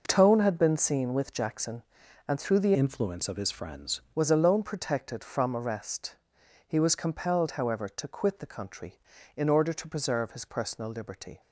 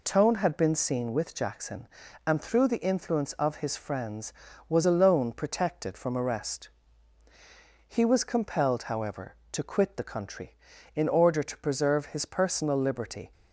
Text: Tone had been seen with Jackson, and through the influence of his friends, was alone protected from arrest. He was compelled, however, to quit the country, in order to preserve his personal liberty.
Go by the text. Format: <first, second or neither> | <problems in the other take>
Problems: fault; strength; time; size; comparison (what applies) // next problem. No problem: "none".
second | changes voice from "influence" to "friends"; from 2.7 to 3.9 s; 1.2 s long